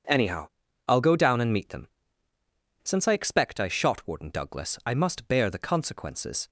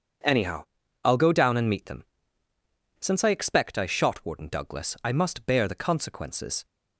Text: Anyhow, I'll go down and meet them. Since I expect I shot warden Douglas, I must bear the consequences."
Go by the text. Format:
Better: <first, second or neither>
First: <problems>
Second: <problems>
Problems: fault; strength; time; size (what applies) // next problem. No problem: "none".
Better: neither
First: none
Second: none